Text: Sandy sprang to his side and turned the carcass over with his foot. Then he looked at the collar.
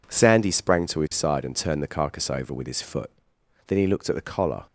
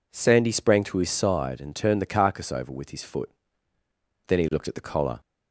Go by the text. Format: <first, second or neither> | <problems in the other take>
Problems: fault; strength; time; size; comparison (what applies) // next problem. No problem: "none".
neither | none